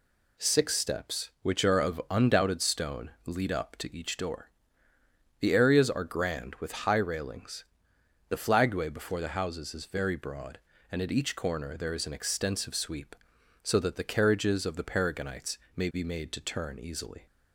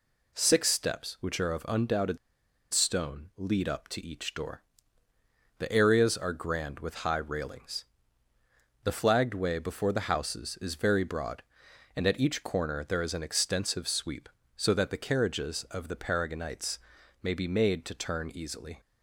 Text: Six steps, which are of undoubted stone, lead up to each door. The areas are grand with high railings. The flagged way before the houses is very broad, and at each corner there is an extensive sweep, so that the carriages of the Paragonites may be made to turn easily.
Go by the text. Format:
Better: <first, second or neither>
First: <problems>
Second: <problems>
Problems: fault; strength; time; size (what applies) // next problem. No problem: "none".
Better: first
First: pauses between "Paragonites" and "may"; slight; at 15.5 s; 0.18 s long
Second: pauses between "undoubted" and "stone"; noticeable; at 2.1 s; 0.53 s long // pauses between "Paragonites" and "may"; at 16.7 s; 0.42 s long